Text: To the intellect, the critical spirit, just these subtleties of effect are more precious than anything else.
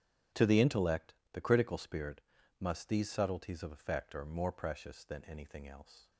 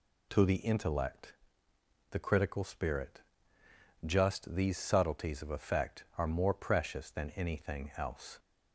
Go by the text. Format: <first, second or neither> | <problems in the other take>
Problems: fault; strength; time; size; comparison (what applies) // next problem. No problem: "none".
second | starts louder than the rest; strong; until 1.5 s; 9.5 dB // says "must" for "just"; at 2.6 s